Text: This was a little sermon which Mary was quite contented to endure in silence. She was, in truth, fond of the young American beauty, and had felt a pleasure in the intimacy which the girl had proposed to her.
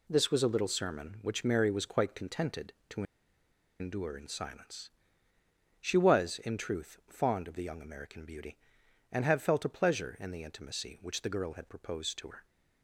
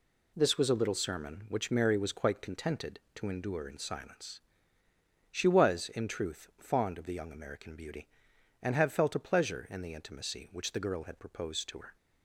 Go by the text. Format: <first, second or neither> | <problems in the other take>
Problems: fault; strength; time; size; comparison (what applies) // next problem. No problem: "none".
second | pauses between "to" and "endure"; noticeable; at 3.0 s; 0.77 s long